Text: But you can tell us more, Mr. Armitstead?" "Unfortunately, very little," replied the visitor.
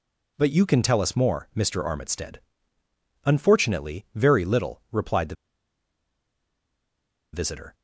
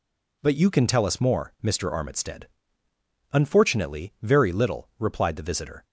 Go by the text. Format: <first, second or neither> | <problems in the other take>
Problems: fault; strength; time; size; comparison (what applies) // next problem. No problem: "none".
second | pauses between "the" and "visitor"; strong; at 5.3 s; 2.0 s long